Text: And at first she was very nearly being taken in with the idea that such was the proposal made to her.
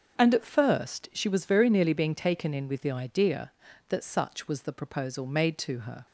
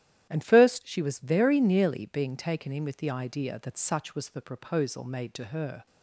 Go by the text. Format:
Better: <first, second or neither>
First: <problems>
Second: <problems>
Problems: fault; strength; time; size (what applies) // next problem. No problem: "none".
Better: first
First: starts louder than the rest; until 1.2 s; 6 dB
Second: starts louder than the rest; strong; until 1.3 s; 12 dB // skips "at"; at 0.4 s